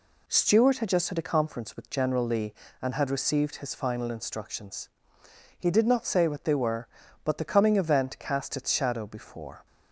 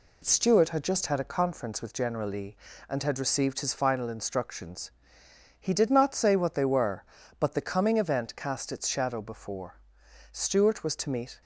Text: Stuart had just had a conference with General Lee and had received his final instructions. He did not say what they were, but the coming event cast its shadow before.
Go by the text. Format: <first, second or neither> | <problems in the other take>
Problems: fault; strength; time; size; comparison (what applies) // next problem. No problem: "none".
first | goes on to say "Stuart was to meet"; noticeable; from 10.3 s on; 1.0 s long